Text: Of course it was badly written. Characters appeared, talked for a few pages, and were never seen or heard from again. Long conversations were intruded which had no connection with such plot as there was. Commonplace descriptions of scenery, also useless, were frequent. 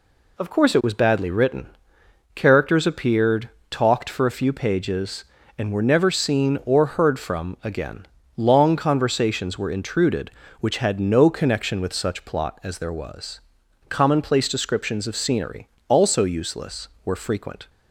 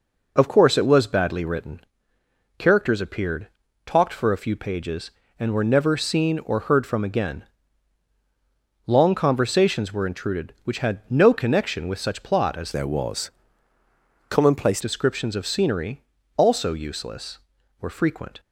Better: first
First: none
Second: changes voice from "there" to "Commonplace"; from 12.7 to 14.7 s; 2.0 s long

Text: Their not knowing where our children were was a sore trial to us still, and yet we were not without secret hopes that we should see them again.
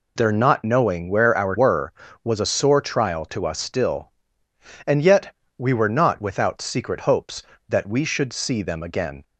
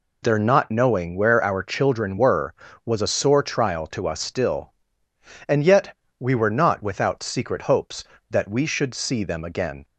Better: second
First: skips "children"; at 1.5 s // pauses between "yet" and "we"; slight; at 5.3 s; 0.24 s long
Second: pauses between "yet" and "we"; slight; at 5.9 s; 0.24 s long

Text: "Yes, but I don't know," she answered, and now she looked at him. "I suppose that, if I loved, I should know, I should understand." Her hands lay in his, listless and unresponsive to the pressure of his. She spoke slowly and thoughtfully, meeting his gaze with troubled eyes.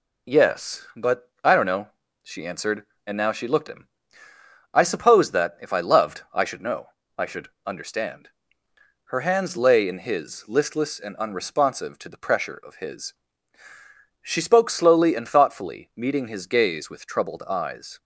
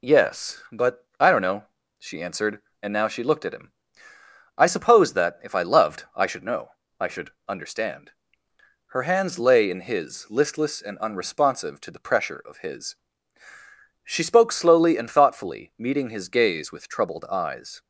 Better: second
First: skips "at"; at 3.6 s // pauses between "should" and "understand"; slight; at 7.4 s; 0.18 s long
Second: pauses between "should" and "understand"; slight; at 7.2 s; 0.18 s long

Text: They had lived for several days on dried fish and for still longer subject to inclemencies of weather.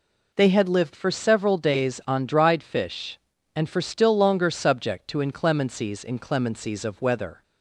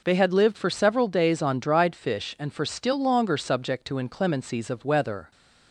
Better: second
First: says "inclemencies" twice; at 6.0 s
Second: none

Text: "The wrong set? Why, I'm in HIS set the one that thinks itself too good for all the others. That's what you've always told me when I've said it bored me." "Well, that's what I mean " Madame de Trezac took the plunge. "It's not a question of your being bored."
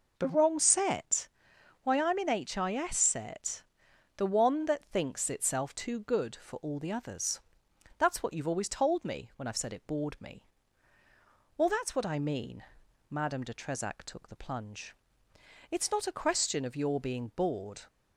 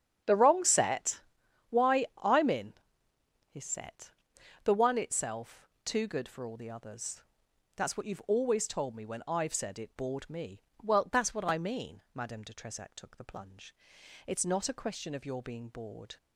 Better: first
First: pauses between "set" and "the"; noticeable; at 3.6 s; 0.52 s long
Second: starts louder than the rest; strong; until 1.7 s; 8.5 dB // pauses between "in" and "HIS"; noticeable; at 2.7 s; 0.76 s long // pauses between "set" and "the"; noticeable; at 4.1 s; 0.52 s long // skips "that thinks"; at 4.9 s // pauses between "itself" and "too"; slight; at 5.6 s; 0.18 s long

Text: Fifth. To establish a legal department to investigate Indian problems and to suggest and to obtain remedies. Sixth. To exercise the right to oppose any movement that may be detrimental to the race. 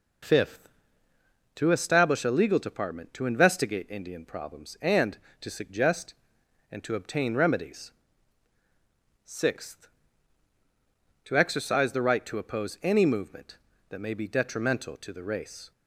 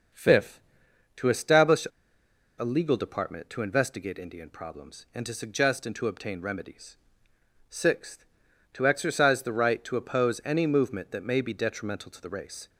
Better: first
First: none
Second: starts louder than the rest; noticeable; until 1.7 s; 6 dB // pauses between "establish" and "a"; noticeable; at 1.8 s; 0.73 s long

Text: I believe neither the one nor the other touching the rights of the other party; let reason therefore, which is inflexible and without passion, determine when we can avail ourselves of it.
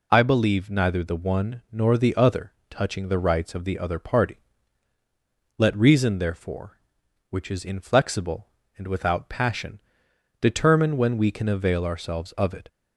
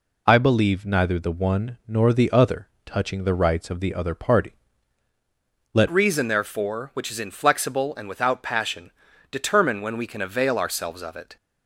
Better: first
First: pauses between "other" and "touching"; slight; at 2.5 s; 0.16 s long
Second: pauses between "other" and "touching"; slight; at 2.6 s; 0.16 s long // changes voice at "reason"; from 5.8 s on; 5.5 s long

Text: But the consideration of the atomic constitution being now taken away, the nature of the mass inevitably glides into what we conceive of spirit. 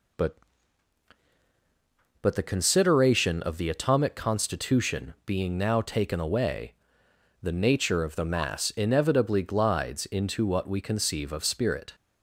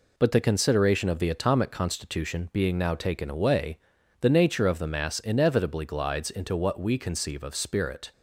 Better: second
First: says "But" twice; at 2.2 s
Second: none

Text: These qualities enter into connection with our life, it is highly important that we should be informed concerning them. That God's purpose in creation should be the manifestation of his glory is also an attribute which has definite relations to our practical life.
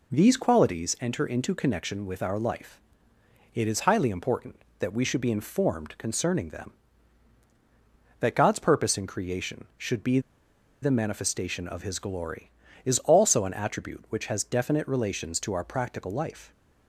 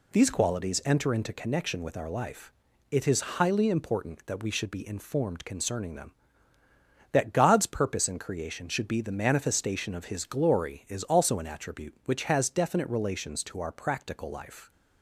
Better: second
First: pauses between "be" and "the"; noticeable; at 10.1 s; 0.62 s long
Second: none

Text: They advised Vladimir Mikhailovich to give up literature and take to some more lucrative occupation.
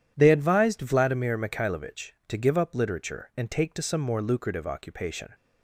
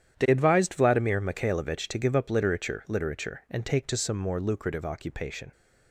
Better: first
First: none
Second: starts louder than the rest; strong; until 1.2 s; 9.5 dB // says "literature" twice; at 2.8 s

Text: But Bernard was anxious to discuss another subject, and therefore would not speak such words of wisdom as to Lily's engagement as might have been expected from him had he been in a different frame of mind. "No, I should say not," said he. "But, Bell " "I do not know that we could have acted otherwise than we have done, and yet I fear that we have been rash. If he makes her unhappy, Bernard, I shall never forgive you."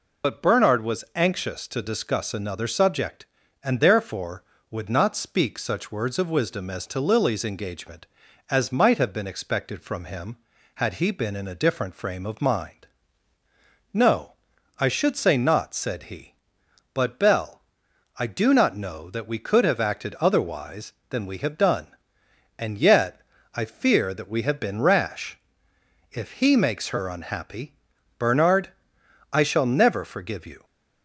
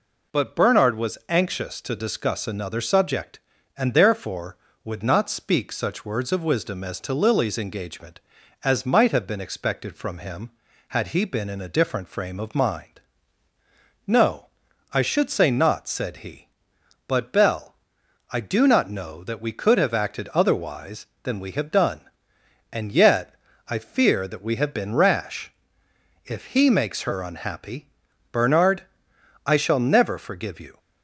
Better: second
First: loses the start of "But"; at 0.2 s; 65 ms // pauses between "yet" and "I"; slight; at 23.2 s; 0.32 s long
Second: pauses between "yet" and "I"; slight; at 23.3 s; 0.32 s long

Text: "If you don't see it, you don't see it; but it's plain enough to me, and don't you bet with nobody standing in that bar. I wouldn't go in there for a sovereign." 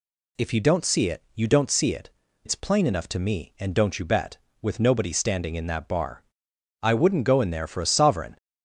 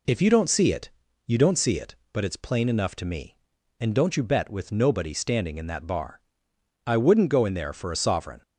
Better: second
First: skips "but"; at 2.2 s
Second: none

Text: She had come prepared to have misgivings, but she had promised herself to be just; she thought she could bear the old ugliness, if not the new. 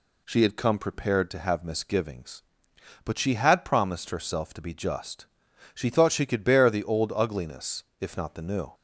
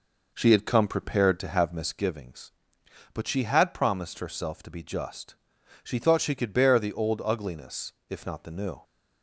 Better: first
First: none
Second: starts louder than the rest; noticeable; until 2.0 s; 5 dB

